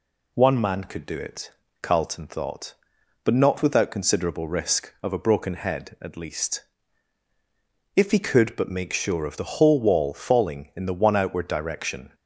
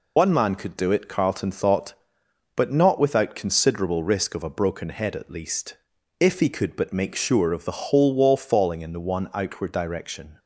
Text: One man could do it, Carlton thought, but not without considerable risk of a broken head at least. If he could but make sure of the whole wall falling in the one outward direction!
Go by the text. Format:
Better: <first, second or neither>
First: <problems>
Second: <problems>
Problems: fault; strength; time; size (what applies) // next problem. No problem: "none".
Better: first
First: none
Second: loses the start of "One"; at 0.1 s; 100 ms